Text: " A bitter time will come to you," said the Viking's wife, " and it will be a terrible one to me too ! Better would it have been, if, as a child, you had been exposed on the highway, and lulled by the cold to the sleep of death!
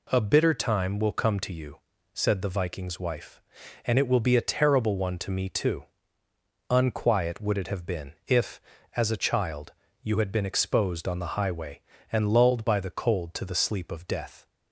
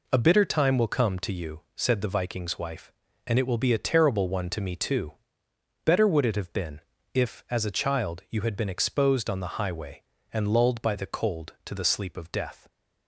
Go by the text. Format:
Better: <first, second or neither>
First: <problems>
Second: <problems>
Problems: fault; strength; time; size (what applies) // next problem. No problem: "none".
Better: second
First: says "Unquiet" for "Better"; at 6.7 s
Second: none